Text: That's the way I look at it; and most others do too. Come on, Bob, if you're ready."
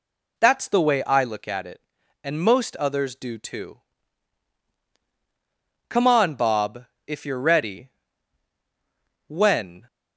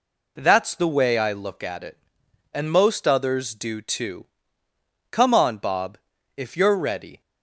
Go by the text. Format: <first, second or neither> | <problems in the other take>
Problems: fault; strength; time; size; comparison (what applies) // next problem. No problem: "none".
second | goes on to say "When"; from 9.2 s on; 0.58 s long